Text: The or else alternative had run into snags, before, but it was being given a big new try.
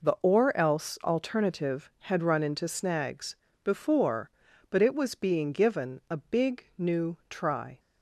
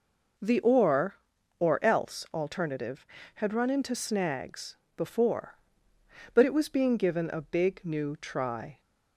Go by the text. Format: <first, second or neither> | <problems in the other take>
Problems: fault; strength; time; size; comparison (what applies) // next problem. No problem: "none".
first | says "or" twice; at 1.5 s